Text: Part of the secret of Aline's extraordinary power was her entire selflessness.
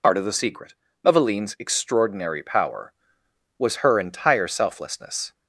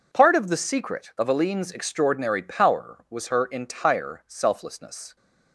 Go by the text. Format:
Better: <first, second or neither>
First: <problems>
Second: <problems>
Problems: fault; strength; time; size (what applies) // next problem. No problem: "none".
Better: second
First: loses the start of "Part"; at 0.0 s; 75 ms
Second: none